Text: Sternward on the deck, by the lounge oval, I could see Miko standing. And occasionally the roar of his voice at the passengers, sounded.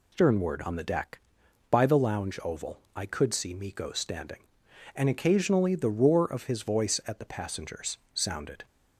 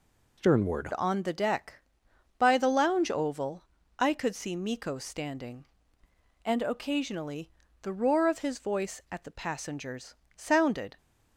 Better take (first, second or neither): first